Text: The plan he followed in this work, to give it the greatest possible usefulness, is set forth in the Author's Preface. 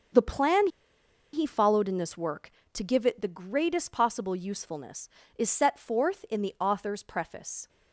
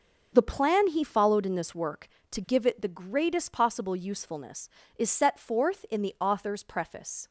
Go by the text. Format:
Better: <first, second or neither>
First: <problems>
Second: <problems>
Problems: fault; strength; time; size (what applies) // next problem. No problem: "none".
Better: second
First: starts louder than the rest; until 1.8 s; 6.5 dB // pauses between "plan" and "he"; noticeable; at 0.6 s; 0.65 s long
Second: starts louder than the rest; until 1.3 s; 6.5 dB